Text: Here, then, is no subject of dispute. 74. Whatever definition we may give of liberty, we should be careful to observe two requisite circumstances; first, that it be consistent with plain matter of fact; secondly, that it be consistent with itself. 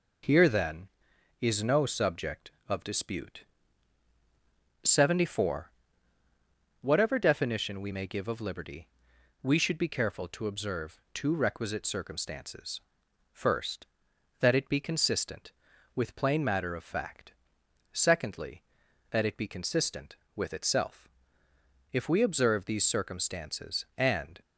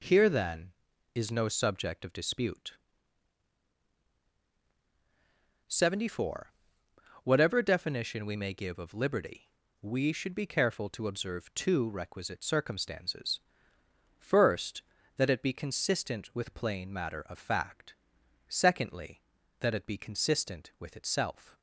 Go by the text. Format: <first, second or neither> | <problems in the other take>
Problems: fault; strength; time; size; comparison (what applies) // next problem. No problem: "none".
second | goes on to say "If we observe these circumstances and"; strong; from 21.9 s on; 2.4 s long